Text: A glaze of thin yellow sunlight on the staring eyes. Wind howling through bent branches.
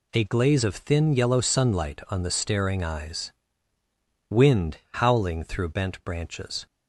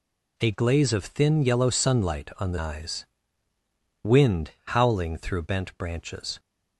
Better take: first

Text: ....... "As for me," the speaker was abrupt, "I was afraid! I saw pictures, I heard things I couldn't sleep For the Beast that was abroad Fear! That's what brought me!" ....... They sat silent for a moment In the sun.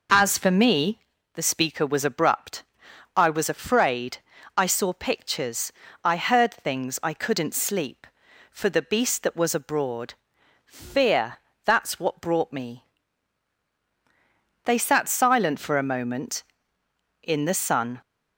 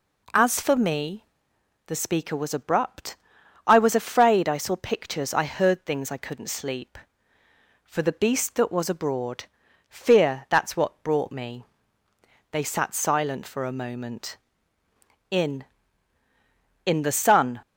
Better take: first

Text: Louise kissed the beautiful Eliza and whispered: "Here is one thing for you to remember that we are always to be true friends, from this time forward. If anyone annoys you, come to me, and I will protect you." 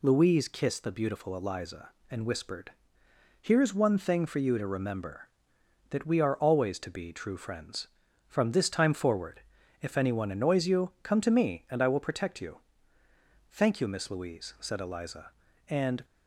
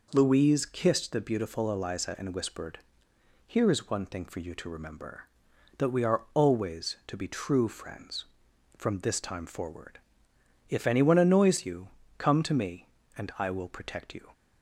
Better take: second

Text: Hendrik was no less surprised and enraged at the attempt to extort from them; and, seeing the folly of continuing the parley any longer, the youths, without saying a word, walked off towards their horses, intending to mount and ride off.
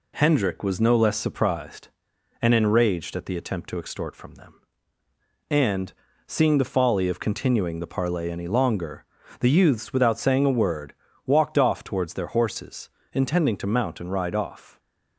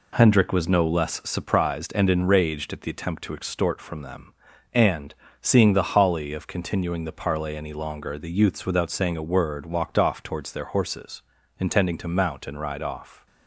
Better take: first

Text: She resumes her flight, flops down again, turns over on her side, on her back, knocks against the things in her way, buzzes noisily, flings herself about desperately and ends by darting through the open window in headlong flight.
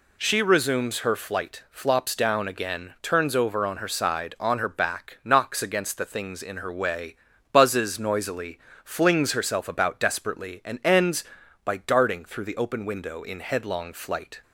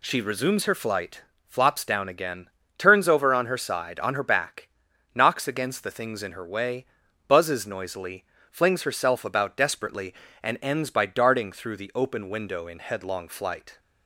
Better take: neither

